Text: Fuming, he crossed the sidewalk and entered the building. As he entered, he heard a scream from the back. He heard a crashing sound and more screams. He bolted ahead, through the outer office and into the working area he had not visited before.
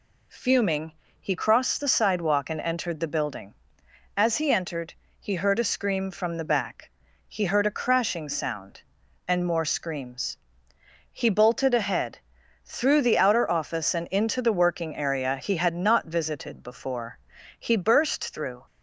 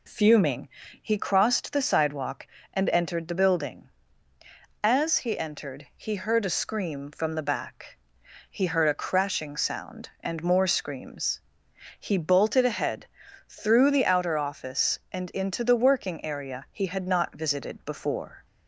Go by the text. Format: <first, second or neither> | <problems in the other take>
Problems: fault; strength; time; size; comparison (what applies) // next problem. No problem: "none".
second | goes on to say "He burst through"; noticeable; from 17.5 s on; 1.0 s long